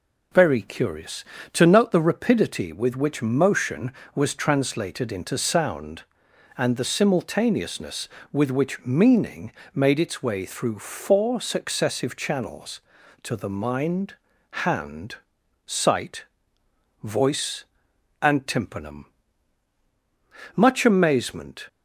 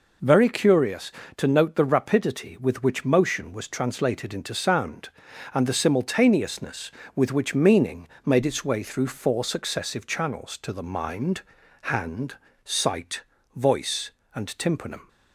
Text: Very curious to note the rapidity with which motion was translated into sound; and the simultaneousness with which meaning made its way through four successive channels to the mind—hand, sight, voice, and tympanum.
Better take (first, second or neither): second